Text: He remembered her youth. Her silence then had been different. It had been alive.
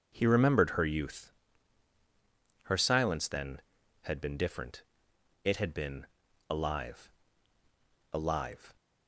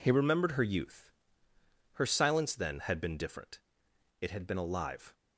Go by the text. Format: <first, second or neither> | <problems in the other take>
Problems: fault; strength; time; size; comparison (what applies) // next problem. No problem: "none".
second | pauses between "been" and "alive"; at 6.0 s; 0.42 s long // says "alive" twice; at 8.1 s